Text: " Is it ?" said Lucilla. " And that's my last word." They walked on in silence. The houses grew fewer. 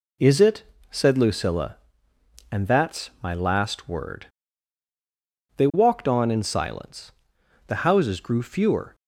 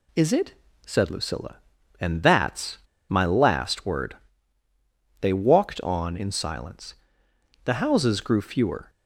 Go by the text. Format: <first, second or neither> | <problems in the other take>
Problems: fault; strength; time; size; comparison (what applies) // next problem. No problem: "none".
first | pauses between "that's" and "my"; slight; at 2.7 s; 0.30 s long